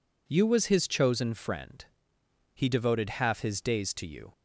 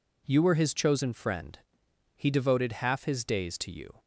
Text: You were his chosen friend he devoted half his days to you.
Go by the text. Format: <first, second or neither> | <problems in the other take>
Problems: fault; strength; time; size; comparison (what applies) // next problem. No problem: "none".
second | says "was" for "were"; at 0.4 s // pauses between "friend" and "he"; noticeable; at 1.8 s; 0.72 s long; noticeable in the second